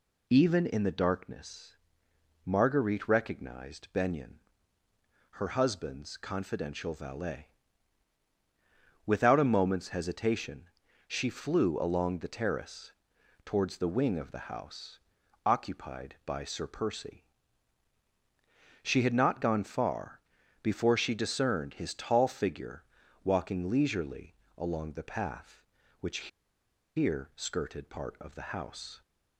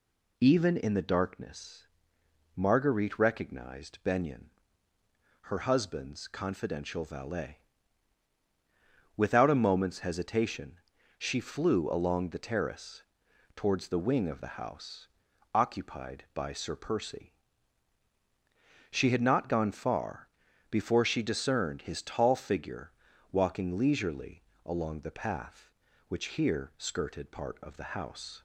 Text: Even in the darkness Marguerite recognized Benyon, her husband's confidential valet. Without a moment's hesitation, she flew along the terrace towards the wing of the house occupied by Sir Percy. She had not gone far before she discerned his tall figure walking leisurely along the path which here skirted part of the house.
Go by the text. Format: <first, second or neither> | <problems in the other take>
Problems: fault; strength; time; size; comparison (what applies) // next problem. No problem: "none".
second | pauses between "darkness" and "Marguerite"; noticeable; at 1.7 s; 0.68 s long; noticeable in the second // pauses between "terrace" and "towards"; noticeable; at 12.9 s; 0.54 s long; noticeable in the second // pauses between "house" and "occupied"; noticeable; at 14.9 s; 0.46 s long; noticeable in the second // pauses between "far" and "before"; at 20.1 s; 0.42 s long; also in the second // pauses between "figure" and "walking"; at 22.8 s; 0.40 s long; also in the second // pauses between "leisurely" and "along"; slight; at 24.3 s; 0.22 s long; slight in the second // pauses between "which" and "here"; noticeable; at 26.2 s; 0.69 s long